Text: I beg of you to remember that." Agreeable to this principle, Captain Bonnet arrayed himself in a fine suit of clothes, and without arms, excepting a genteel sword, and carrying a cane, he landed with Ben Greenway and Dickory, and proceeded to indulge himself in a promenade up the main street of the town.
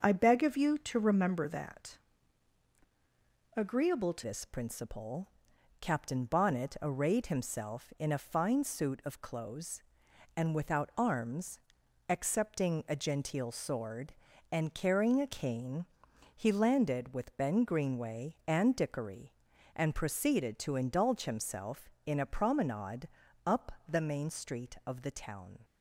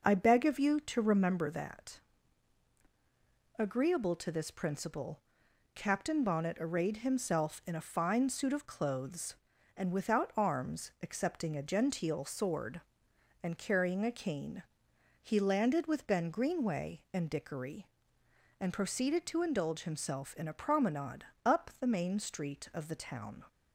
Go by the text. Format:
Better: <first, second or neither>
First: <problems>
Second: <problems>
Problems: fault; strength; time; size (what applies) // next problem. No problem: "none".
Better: second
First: starts louder than the rest; noticeable; until 1.0 s; 6 dB // changes voice at "this"; from 4.2 s on; 21.4 s long // pauses between "promenade" and "up"; at 23.0 s; 0.38 s long // pauses between "up" and "the"; slight; at 23.7 s; 0.18 s long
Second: pauses between "promenade" and "up"; slight; at 21.2 s; 0.20 s long